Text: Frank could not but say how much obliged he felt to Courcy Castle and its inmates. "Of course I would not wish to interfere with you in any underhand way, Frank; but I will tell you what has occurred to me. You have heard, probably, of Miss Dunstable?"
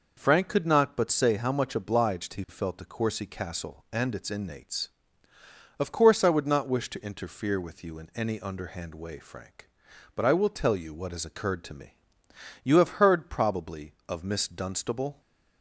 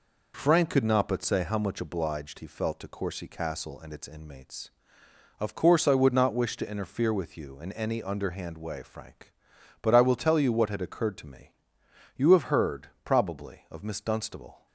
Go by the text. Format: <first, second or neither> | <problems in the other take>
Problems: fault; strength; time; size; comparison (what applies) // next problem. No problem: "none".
first | says "had" for "has"; at 10.7 s